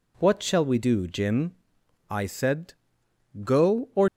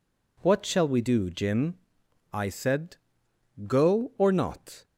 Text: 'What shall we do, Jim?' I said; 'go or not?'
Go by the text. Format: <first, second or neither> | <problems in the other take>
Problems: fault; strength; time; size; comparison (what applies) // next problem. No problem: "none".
second | stops before "not"; at 4.0 s